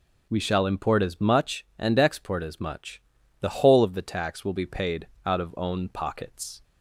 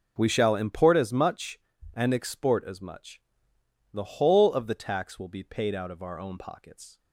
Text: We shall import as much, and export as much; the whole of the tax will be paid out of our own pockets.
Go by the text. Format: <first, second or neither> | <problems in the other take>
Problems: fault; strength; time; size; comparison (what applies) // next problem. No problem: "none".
second | pauses between "paid" and "out"; slight; at 5.0 s; 0.18 s long // skips "our"; at 5.5 s